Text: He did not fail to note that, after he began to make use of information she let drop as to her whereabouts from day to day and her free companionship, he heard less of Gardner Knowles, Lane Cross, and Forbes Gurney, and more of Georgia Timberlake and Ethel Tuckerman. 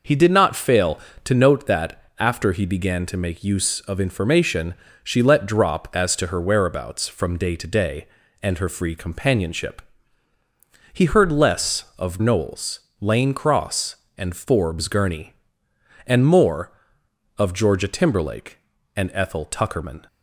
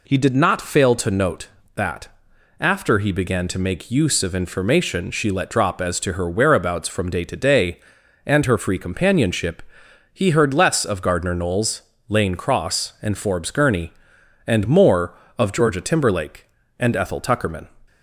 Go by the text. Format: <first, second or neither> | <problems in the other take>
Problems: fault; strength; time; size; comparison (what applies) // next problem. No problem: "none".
second | pauses between "information" and "she"; slight; at 4.7 s; 0.28 s long // skips "Gardner"; at 12.1 s